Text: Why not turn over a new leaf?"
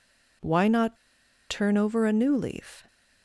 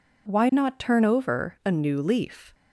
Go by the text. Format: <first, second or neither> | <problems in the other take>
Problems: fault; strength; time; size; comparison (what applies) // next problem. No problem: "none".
second | pauses between "not" and "turn"; noticeable; at 0.9 s; 0.55 s long